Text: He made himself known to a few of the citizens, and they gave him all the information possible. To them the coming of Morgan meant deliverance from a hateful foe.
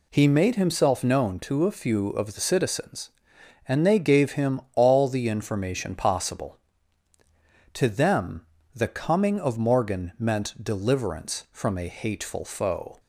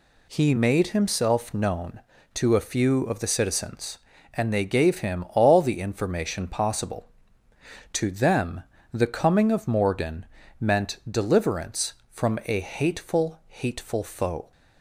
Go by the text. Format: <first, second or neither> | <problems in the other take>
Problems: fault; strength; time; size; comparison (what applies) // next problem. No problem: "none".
first | pauses between "them" and "the"; slight; at 8.6 s; 0.28 s long; slight in the first // pauses between "Morgan" and "meant"; slight; at 10.2 s; 0.34 s long // says "hateful" twice; at 13.4 s